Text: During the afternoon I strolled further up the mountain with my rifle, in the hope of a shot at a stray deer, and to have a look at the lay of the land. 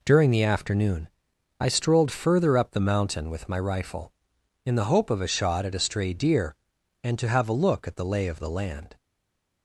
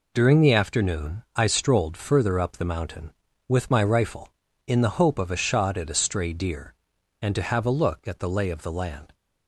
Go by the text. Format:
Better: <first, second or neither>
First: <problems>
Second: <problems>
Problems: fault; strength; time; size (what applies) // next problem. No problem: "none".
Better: second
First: pauses between "afternoon" and "I"; noticeable; at 1.0 s; 0.50 s long // stays silent after the last word; slight; from 8.9 s on; 0.7 s long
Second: none